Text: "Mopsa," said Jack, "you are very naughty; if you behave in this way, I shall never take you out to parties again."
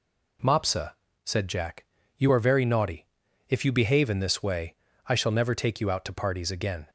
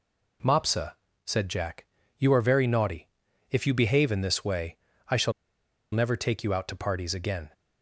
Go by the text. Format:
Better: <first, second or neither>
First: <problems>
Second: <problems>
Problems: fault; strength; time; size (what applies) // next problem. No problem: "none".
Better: first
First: none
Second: pauses between "shall" and "never"; noticeable; at 5.3 s; 0.62 s long